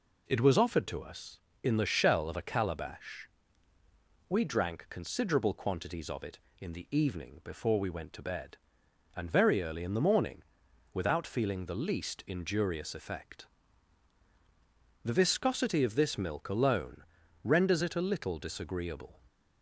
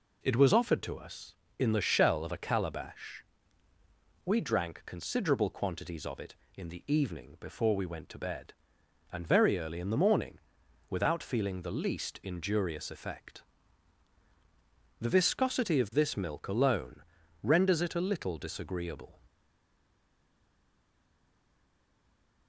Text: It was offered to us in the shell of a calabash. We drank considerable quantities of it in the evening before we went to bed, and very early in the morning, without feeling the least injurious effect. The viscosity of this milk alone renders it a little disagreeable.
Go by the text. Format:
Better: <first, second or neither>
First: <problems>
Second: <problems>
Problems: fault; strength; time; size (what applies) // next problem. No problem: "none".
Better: first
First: pauses between "alone" and "renders"; at 17.0 s; 0.40 s long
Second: pauses between "alone" and "renders"; at 17.0 s; 0.40 s long // stays silent after the last word; strong; from 19.2 s on; 3.2 s long